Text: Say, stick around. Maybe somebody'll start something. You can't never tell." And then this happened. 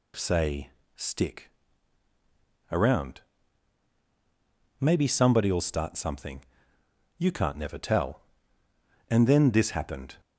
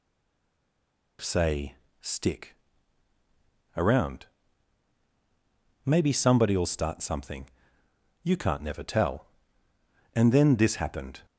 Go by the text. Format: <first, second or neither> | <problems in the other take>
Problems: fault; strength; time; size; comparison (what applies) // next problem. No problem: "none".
first | stays silent before the first word; noticeable; until 1.1 s; 1.1 s long // pauses between "stick" and "around"; at 2.5 s; 1.2 s long; also in the first